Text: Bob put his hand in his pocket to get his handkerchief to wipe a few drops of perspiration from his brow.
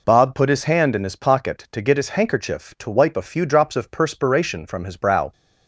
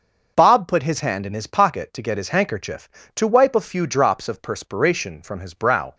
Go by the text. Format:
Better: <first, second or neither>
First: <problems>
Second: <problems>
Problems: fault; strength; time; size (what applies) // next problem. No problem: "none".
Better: neither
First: none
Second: none